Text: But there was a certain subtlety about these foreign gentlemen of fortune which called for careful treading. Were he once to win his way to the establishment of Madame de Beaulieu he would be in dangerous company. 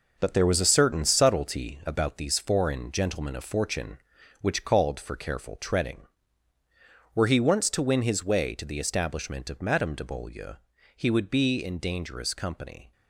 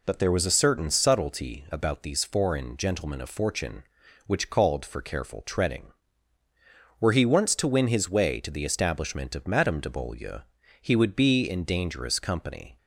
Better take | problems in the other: second | gets quieter; strong; throughout; 7.5 dB // pauses between "Beaulieu" and "he"; at 10.5 s; 0.42 s long; also in the second

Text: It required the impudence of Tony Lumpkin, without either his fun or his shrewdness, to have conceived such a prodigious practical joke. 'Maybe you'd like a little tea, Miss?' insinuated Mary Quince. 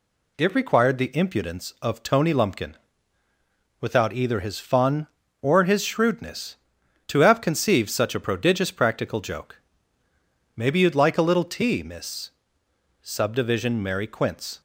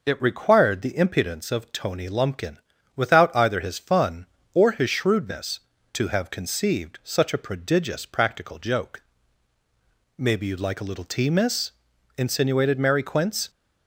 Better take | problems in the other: second | says "subdivision" for "insinuated"; at 13.0 s

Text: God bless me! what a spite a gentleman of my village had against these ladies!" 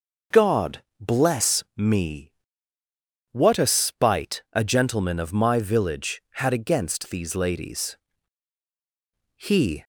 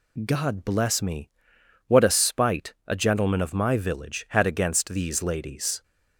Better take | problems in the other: second | pauses between "God" and "bless"; slight; at 0.8 s; 0.16 s long // goes on to say "He"; slight; from 9.3 s on; 0.48 s long

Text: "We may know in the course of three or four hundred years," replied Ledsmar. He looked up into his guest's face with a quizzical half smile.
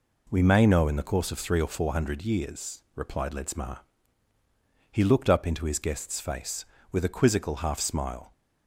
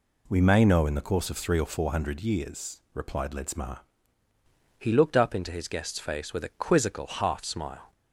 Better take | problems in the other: first | changes voice at "He"; from 4.7 s on; 3.2 s long

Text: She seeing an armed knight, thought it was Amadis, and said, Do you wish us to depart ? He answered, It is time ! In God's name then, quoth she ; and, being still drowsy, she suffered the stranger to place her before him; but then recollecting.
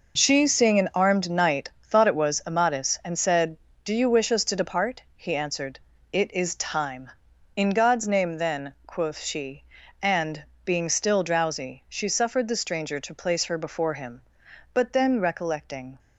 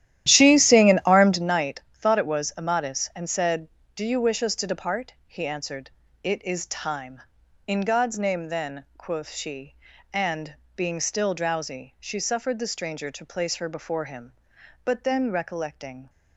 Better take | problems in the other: first | starts louder than the rest; strong; until 1.5 s; 12 dB

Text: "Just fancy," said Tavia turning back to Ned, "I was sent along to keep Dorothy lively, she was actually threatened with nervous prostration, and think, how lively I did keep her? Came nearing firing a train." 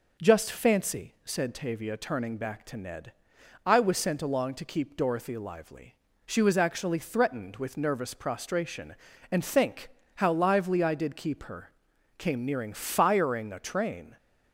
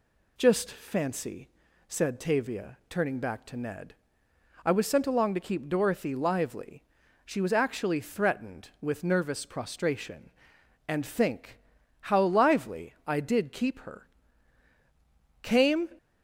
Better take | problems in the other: first | stops before "nearing firing a train"; at 15.9 s

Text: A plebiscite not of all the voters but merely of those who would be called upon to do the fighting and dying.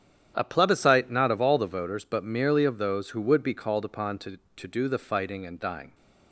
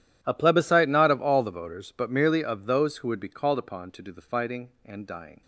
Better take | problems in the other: second | starts louder than the rest; strong; until 1.3 s; 10 dB // says "to" twice; at 4.5 s

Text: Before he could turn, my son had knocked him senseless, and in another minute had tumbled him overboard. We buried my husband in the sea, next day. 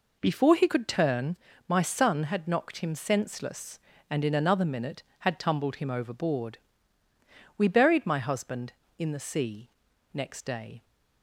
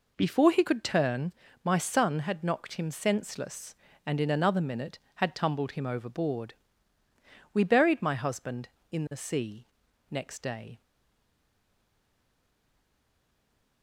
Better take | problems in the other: first | stays silent after the last word; strong; from 10.8 s on; 3.0 s long

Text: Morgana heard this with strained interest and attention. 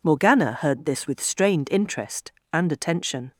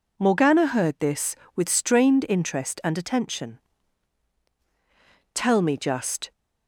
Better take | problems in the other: first | goes on to say "Tell me just"; noticeable; from 5.3 s on; 0.98 s long

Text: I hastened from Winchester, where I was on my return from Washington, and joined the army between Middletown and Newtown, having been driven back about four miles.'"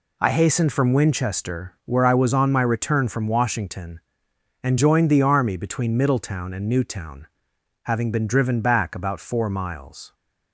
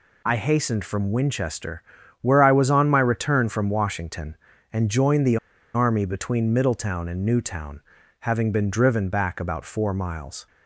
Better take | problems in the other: first | pauses between "the" and "army"; at 5.3 s; 0.37 s long

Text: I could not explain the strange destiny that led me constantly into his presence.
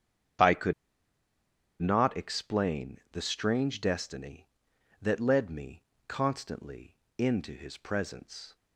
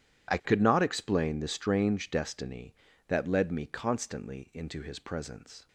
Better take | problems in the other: second | starts louder than the rest; strong; until 2.5 s; 8 dB // pauses between "could" and "not"; at 0.7 s; 1.0 s long // pauses between "me" and "constantly"; slight; at 5.8 s; 0.24 s long // pauses between "constantly" and "into"; slight; at 6.9 s; 0.22 s long

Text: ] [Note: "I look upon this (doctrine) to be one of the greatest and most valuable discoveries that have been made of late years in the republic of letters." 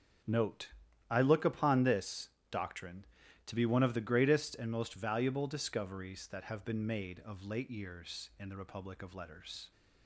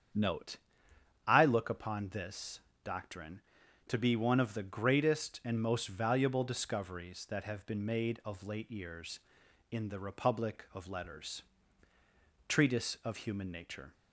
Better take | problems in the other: first | starts louder than the rest; strong; until 1.8 s; 8 dB; strong in the first // goes on to say "Treatise of Human Nature"; from 12.4 s on; 1.4 s long

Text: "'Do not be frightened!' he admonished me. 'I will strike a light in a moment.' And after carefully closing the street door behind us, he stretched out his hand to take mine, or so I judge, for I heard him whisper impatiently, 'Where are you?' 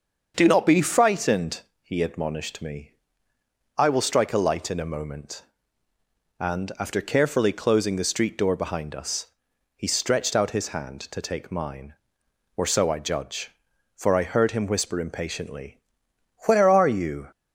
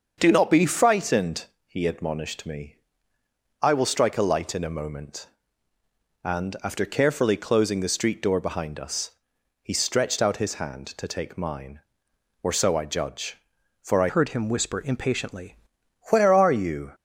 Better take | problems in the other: first | starts louder than the rest; until 1.1 s; 6.5 dB; also in the first // changes voice from "heard" to "impatiently"; from 14.0 to 15.5 s; 1.5 s long

